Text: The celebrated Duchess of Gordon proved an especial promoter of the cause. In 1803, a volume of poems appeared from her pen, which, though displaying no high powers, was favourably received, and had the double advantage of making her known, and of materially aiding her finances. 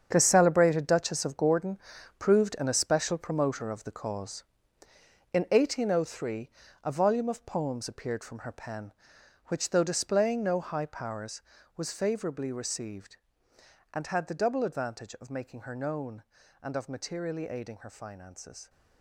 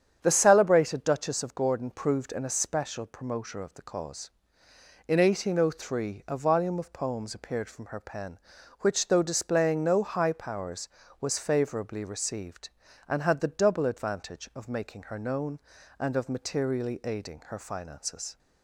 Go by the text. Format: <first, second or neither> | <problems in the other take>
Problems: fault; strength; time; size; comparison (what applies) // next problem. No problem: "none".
second | gets quieter; strong; throughout; 11.5 dB // starts louder than the rest; strong; until 1.1 s; 7.5 dB; strong in the second // pauses between "Gordon" and "proved"; at 1.7 s; 0.42 s long